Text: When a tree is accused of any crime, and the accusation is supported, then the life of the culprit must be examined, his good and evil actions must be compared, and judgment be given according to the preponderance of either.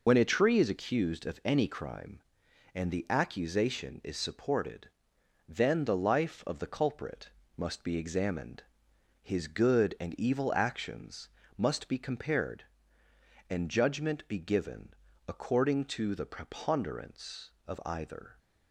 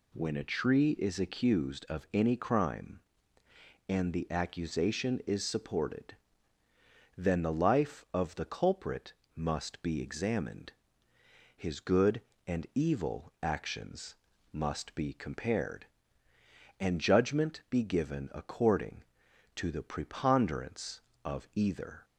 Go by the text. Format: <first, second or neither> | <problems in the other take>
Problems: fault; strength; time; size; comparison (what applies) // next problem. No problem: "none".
second | loses the start of "When"; at 0.0 s; 75 ms // pauses between "culprit" and "must"; slight; at 7.2 s; 0.30 s long; slight in the second // pauses between "actions" and "must"; slight; at 11.2 s; 0.30 s long; slight in the second // pauses between "given" and "according"; slight; at 14.9 s; 0.34 s long